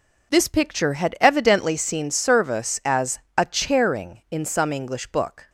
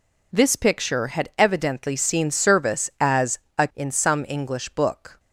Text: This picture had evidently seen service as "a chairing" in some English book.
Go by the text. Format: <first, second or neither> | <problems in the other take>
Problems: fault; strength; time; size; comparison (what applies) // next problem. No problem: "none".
first | pauses between "as" and "a"; slight; at 3.3 s; 0.20 s long; slight in the first // skips "chairing"; at 3.7 s